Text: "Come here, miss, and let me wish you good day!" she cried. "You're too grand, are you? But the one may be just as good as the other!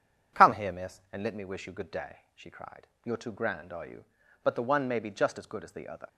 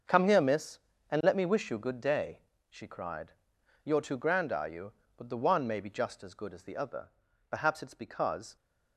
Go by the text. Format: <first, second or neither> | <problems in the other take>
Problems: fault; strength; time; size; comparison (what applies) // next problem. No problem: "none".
first | starts louder than the rest; until 1.4 s; 6.5 dB // goes on to say "Perhaps it's because"; noticeable; from 7.4 s on; 1.0 s long